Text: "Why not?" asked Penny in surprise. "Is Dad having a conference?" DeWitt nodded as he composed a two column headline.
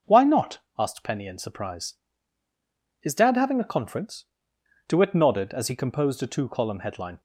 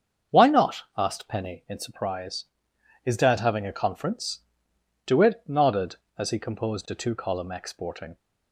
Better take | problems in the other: first | starts louder than the rest; until 1.4 s; 7 dB // says "exporting" for "headline"; at 7.5 s

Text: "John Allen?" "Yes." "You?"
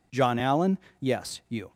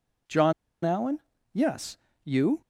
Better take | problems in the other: first | pauses between "John" and "Allen"; slight; at 0.5 s; 0.31 s long

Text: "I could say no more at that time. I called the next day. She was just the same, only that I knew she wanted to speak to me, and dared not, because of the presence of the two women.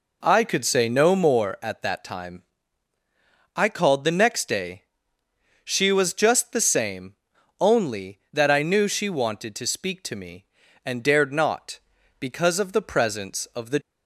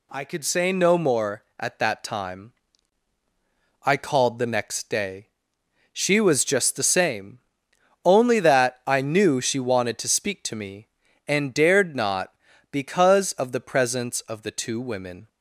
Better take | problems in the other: second | stops before "two women"; at 13.8 s

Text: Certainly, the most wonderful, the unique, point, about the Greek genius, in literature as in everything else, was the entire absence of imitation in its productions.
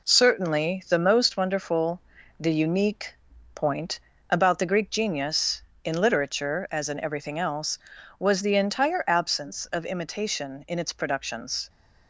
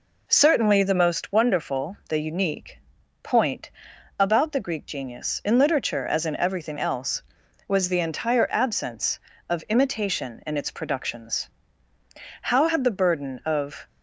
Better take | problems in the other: first | goes on to say "How had the burden of"; from 12.4 s on; 1.4 s long

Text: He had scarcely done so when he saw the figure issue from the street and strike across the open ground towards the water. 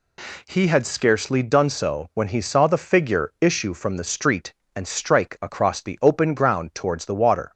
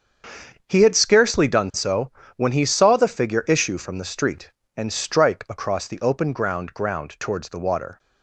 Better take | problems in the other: first | starts louder than the rest; until 1.6 s; 7 dB // pauses between "so" and "when"; slight; at 2.1 s; 0.24 s long // says "ground" twice; at 6.7 s

